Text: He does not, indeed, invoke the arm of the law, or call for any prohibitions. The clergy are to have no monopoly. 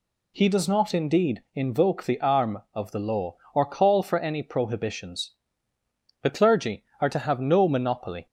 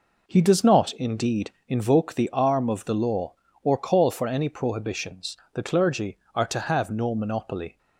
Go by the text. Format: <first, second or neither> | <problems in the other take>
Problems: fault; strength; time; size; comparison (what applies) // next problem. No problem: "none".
neither | none